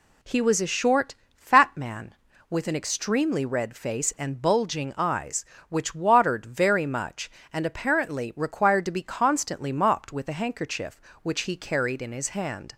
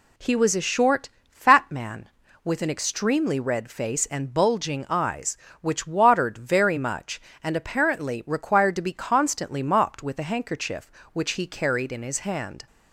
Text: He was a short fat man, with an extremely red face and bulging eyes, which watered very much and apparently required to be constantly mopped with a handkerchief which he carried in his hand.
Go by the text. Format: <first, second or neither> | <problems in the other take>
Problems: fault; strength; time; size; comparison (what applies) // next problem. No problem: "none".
neither | pauses between "short" and "fat"; slight; the same in both